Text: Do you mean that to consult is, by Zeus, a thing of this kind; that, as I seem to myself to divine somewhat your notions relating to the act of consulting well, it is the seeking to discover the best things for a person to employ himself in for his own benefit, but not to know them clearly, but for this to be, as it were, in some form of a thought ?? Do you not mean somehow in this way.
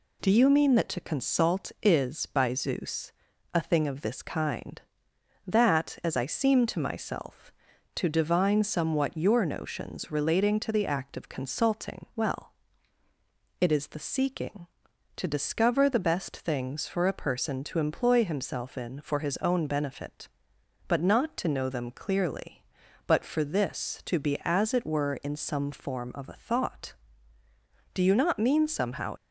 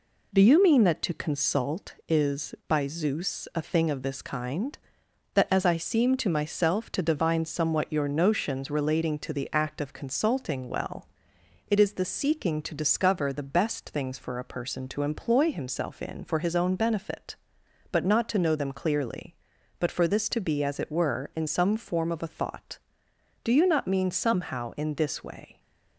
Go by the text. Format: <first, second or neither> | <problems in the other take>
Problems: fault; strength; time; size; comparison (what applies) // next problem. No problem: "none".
second | stops before "in this way"; at 29.1 s